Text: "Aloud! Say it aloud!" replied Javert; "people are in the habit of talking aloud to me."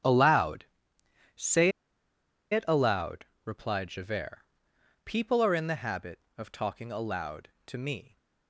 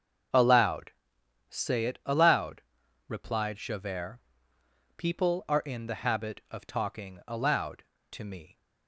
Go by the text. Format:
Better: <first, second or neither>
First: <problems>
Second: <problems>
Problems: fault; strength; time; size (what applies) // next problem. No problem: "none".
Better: second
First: starts louder than the rest; strong; until 2.5 s; 9.5 dB // pauses between "Say" and "it"; noticeable; at 1.7 s; 0.80 s long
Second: starts louder than the rest; until 1.9 s; 6.5 dB